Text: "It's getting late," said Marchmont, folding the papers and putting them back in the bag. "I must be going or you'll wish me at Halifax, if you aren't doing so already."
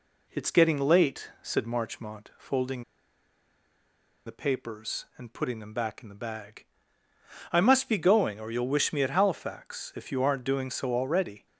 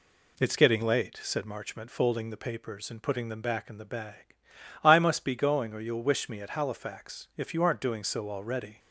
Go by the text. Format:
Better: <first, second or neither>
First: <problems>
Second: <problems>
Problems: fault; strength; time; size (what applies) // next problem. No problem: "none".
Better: second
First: pauses between "folding" and "the"; strong; at 2.8 s; 1.4 s long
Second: none